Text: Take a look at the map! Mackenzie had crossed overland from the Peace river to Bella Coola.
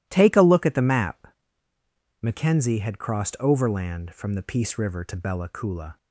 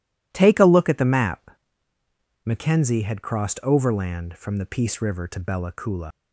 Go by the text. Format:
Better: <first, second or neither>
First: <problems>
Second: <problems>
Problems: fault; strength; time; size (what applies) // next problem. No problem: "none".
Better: first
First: none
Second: leaves "Coola" unfinished; at 6.1 s; 95 ms